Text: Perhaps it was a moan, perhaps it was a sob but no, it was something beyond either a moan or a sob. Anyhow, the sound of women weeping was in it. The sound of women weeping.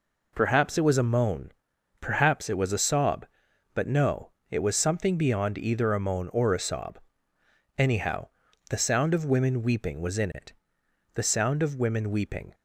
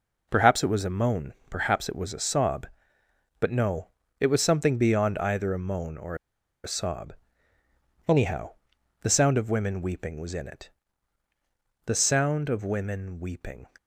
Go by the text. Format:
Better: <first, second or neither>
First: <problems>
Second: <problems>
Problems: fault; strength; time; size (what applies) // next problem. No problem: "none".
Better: first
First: none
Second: pauses between "or" and "a"; noticeable; at 6.1 s; 0.48 s long